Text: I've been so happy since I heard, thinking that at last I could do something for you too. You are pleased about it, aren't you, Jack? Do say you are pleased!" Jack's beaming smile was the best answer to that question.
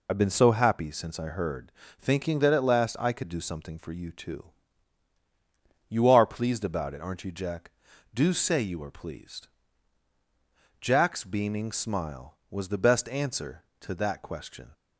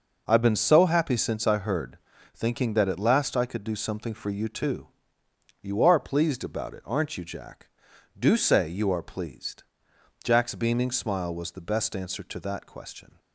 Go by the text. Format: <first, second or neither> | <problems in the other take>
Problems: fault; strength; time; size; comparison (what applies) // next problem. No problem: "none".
second | loses the start of "I've"; at 0.0 s; 60 ms